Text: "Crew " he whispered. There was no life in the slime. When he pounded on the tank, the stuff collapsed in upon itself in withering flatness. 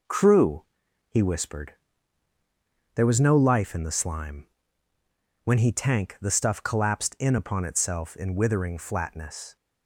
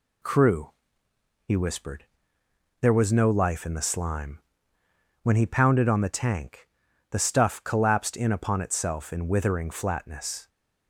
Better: second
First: skips "pounded on the"; at 5.7 s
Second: none

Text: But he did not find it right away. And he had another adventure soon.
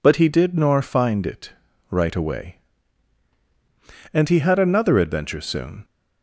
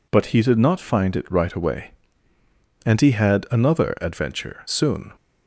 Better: second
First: says "nor" for "not"; at 0.5 s // pauses between "it" and "right"; at 1.5 s; 0.38 s long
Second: none

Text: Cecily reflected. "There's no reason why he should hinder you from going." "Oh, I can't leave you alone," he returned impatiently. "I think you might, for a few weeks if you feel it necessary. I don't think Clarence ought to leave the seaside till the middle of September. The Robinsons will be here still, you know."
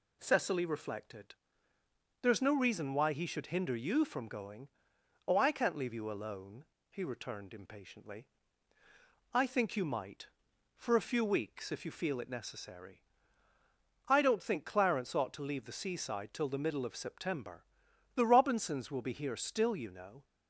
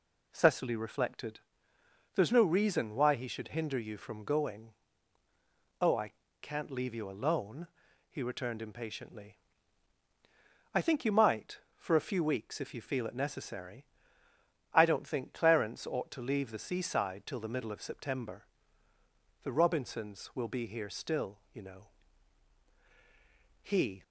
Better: first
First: none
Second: pauses between "I" and "can't"; slight; at 6.1 s; 0.28 s long // goes on to say "He"; slight; from 23.6 s on; 0.40 s long

